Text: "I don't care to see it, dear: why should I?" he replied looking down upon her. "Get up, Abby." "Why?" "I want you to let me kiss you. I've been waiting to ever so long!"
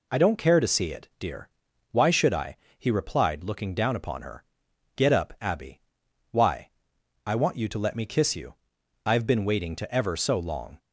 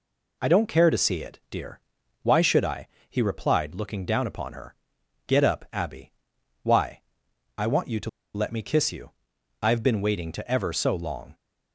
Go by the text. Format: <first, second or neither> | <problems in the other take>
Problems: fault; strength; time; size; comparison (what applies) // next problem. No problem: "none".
first | pauses between "to" and "let"; slight; at 8.0 s; 0.25 s long